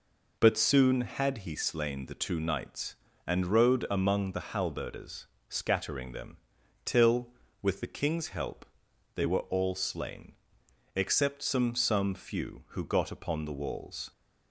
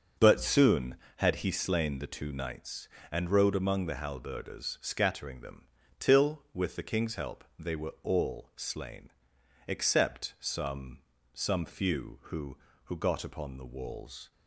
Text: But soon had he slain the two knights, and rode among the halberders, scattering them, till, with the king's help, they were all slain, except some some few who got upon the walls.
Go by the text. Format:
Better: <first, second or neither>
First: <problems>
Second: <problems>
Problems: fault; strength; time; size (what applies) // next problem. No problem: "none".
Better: first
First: none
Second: starts louder than the rest; until 1.3 s; 6.5 dB // pauses between "some" and "some"; slight; at 10.9 s; 0.34 s long // says "who" twice; at 12.8 s